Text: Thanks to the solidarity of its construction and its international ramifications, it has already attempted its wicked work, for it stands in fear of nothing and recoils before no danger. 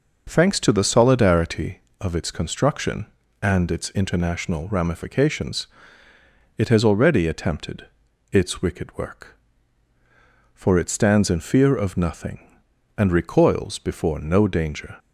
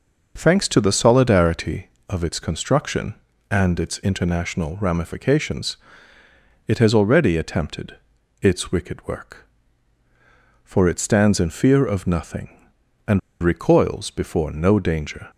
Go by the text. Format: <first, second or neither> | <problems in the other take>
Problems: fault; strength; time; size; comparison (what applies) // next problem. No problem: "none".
first | pauses between "attempted" and "its"; noticeable; at 7.9 s; 0.46 s long; noticeable in the first // pauses between "and" and "recoils"; slight; at 13.1 s; 0.23 s long